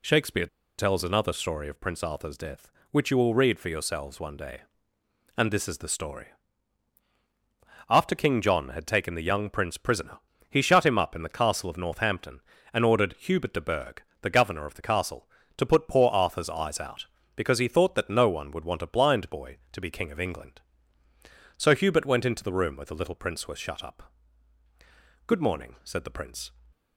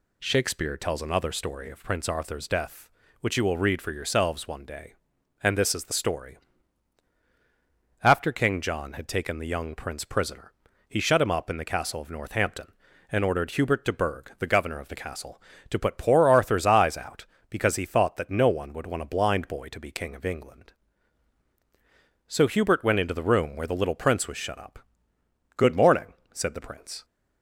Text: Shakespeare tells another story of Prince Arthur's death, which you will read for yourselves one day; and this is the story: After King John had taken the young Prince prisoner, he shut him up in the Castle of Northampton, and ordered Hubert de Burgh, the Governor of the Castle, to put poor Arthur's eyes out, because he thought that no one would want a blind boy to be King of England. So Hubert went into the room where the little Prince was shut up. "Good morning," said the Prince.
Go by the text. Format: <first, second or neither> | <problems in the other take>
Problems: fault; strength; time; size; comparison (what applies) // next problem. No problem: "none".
second | pauses between "Shakespeare" and "tells"; slight; at 0.4 s; 0.32 s long